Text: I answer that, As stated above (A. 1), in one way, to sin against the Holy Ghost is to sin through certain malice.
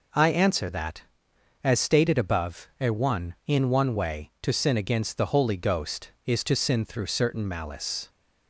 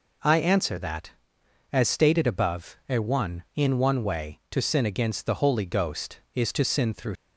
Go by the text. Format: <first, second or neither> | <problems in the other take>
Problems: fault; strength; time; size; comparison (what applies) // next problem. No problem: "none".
first | stops before "certain malice"; at 7.1 s